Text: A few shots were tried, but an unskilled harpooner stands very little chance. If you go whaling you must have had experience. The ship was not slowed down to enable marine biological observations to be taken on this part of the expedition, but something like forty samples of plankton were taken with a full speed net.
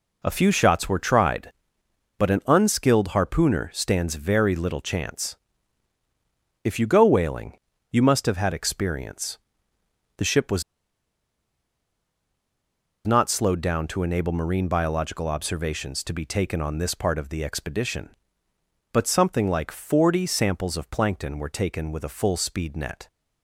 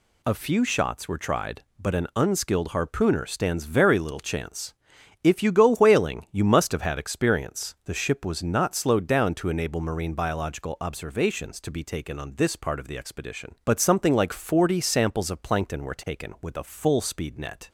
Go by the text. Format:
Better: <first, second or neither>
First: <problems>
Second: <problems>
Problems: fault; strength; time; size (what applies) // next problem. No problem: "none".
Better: second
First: pauses between "whaling" and "you"; slight; at 7.5 s; 0.34 s long // pauses between "was" and "not"; strong; at 10.6 s; 2.4 s long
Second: none